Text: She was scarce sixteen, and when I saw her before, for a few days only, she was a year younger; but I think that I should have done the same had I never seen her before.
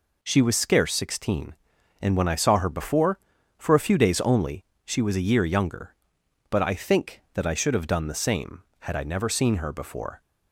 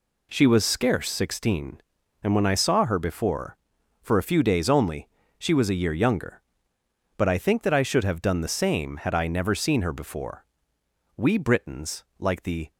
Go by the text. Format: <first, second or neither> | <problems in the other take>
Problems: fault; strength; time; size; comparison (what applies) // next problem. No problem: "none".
first | goes on to say "We Britons like the"; from 11.1 s on; 1.5 s long